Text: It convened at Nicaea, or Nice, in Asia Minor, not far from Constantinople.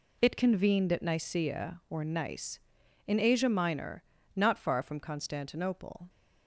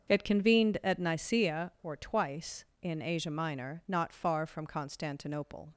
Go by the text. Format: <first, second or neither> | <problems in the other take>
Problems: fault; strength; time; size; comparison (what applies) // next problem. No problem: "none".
first | starts louder than the rest; until 1.1 s; 7 dB // says "Twice" for "Nice"; at 1.9 s